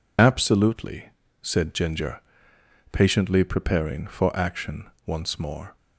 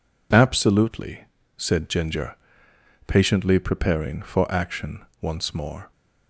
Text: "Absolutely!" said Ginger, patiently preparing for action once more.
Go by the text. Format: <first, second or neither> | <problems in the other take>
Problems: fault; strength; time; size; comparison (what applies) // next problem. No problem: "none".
second | loses the start of "Absolutely"; at 0.1 s; 35 ms // pauses between "action" and "once"; slight; at 4.8 s; 0.18 s long; slight in the second